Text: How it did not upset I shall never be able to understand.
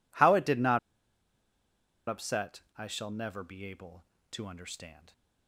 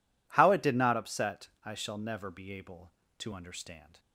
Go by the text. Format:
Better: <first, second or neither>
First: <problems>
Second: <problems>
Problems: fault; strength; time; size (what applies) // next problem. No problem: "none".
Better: second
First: pauses between "not" and "upset"; strong; at 0.7 s; 1.2 s long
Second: none